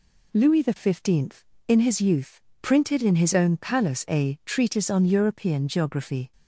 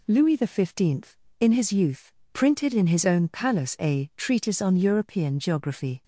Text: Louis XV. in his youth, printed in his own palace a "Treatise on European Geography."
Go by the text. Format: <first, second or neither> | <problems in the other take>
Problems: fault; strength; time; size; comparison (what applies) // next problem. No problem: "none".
neither | none